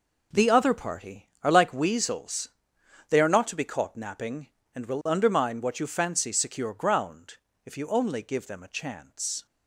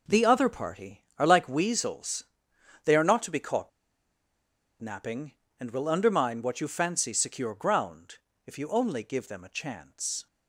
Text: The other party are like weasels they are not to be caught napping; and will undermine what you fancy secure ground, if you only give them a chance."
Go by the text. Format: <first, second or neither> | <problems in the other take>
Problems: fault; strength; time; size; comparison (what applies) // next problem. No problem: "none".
first | pauses between "weasels" and "they"; noticeable; at 2.2 s; 0.62 s long; noticeable in the first // pauses between "caught" and "napping"; at 3.6 s; 1.1 s long